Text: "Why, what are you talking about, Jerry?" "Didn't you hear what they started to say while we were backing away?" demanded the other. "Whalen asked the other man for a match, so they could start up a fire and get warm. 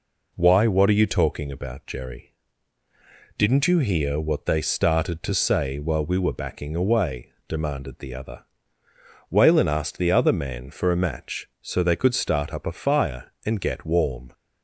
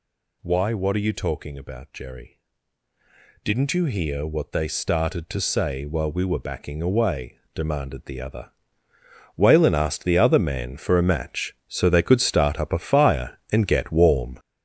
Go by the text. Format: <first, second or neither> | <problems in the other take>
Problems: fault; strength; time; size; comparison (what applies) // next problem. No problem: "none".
first | gets louder; strong; throughout; 7.5 dB